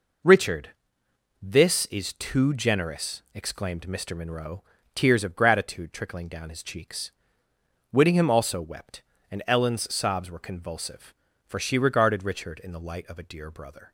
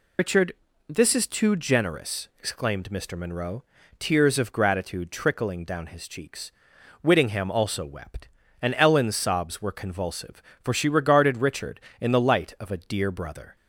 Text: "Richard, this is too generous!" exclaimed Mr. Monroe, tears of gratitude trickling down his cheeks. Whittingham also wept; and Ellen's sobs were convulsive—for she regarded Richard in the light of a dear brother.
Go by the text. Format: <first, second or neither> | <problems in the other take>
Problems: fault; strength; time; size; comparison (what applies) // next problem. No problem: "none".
first | loses the start of "Richard"; at 0.1 s; 80 ms